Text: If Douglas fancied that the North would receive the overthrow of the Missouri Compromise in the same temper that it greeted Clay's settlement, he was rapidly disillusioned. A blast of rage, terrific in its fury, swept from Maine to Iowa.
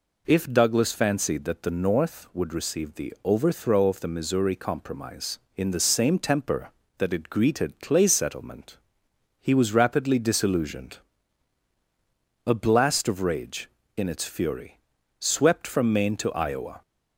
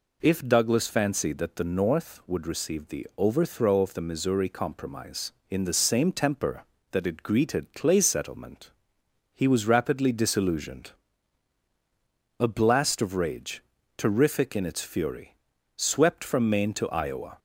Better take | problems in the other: second | skips "terrific"; at 13.8 s

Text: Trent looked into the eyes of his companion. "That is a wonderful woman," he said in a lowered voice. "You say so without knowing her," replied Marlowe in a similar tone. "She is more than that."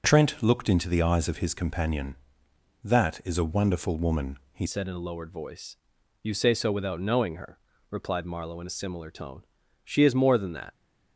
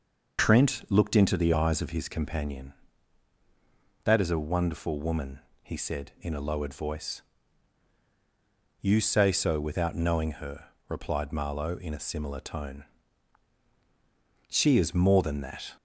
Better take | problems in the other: second | changes voice at "said"; from 4.6 s on; 6.1 s long

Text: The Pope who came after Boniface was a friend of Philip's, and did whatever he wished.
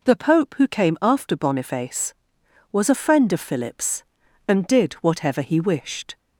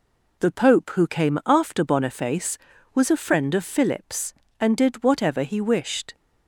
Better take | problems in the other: neither | none

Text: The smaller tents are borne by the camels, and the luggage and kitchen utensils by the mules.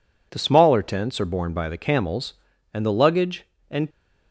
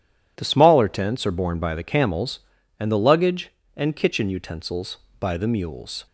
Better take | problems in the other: second | stops before "kitchen utensils by the mules"; at 3.8 s

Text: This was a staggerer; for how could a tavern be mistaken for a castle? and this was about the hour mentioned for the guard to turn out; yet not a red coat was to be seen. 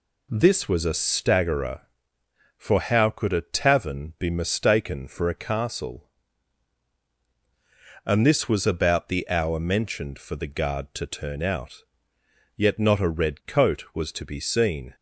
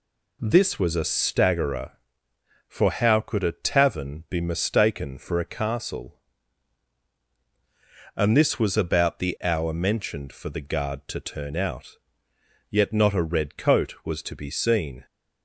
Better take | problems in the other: neither | none

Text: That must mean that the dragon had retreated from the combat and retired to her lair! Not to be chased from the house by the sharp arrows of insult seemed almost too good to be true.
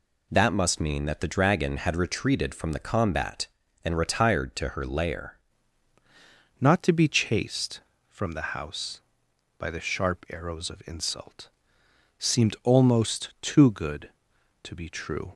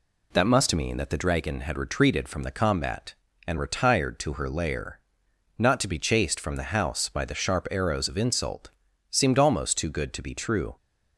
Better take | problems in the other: second | changes voice at "Not"; from 6.5 s on; 8.8 s long // pauses between "insult" and "seemed"; noticeable; at 11.4 s; 0.70 s long; also in the second

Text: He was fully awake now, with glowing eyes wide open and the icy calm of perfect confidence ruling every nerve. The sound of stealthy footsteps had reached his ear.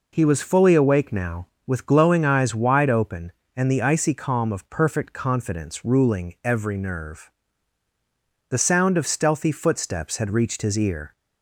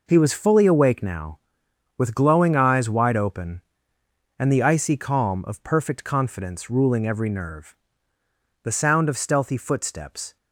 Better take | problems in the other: first | stops before "had reached his ear"; at 10.3 s

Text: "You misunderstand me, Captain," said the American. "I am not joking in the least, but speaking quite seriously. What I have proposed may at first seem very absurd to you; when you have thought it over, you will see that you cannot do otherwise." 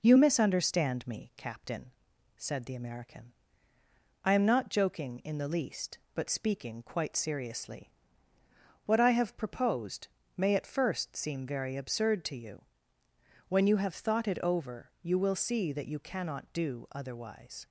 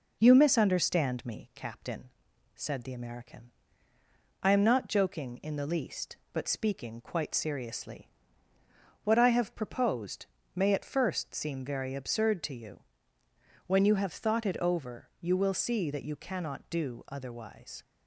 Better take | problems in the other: neither | pauses between "proposed" and "may"; slight; the same in both

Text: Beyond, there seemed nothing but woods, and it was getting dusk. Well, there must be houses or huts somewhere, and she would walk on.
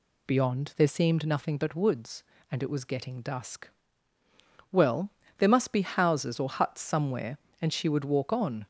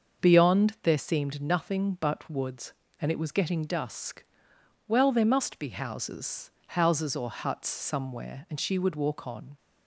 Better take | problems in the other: first | starts louder than the rest; until 1.2 s; 6.5 dB // says "houses" twice; at 6.6 s

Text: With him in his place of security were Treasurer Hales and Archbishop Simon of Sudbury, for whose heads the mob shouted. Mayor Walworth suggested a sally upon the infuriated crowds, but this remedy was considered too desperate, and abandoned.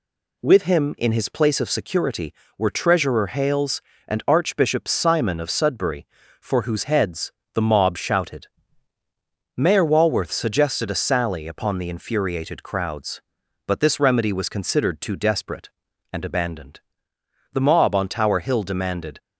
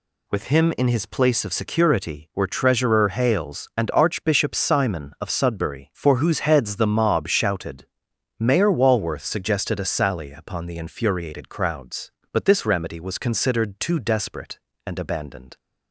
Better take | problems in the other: second | pauses between "heads" and "the"; slight; at 7.3 s; 0.22 s long // goes on to say "The mob on Tower Hill demanded"; from 17.5 s on; 1.6 s long

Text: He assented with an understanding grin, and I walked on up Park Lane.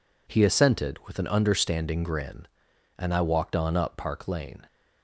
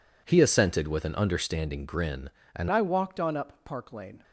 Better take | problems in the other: first | changes voice at "I"; from 2.7 s on; 1.5 s long

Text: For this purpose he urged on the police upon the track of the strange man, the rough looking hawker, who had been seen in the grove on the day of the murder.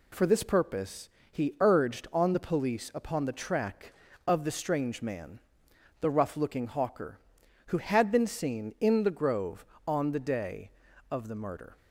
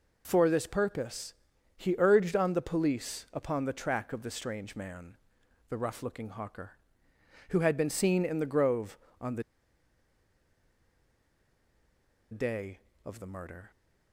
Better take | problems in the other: first | pauses between "purpose" and "he"; at 1.3 s; 0.44 s long; slight in the first // pauses between "the" and "day"; strong; at 9.4 s; 2.8 s long

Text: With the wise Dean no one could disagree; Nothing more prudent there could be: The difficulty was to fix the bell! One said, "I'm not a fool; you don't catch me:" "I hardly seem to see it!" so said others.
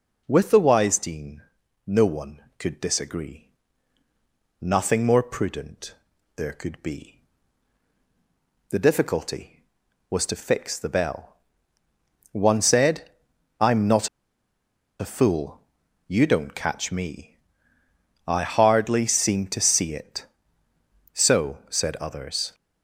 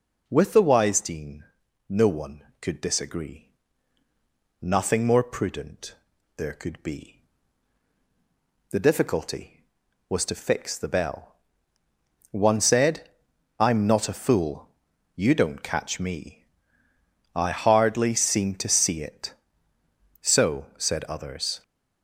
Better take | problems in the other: second | pauses between "Dean" and "no"; at 1.4 s; 0.44 s long; also in the second // pauses between "prudent" and "there"; at 5.9 s; 0.42 s long; also in the second // pauses between "not" and "a"; noticeable; at 14.0 s; 0.91 s long

